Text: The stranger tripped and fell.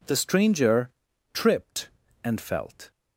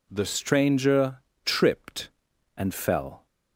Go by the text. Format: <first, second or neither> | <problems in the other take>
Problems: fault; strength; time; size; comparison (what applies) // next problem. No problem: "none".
second | pauses between "stranger" and "tripped"; at 0.9 s; 0.42 s long; slight in the second // says "felt" for "fell"; at 2.4 s